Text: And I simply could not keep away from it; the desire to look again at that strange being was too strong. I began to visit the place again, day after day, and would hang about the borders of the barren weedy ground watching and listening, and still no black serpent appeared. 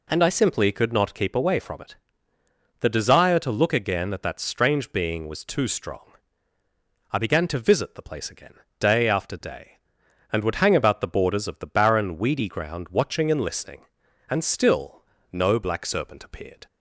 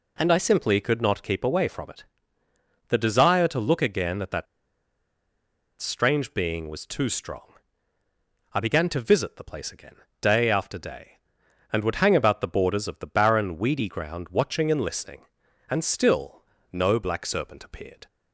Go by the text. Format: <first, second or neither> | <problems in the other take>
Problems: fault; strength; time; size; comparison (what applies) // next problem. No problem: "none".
first | pauses between "that" and "strange"; strong; at 4.4 s; 1.3 s long // pauses between "still" and "no"; slight; at 16.4 s; 0.28 s long; slight in the first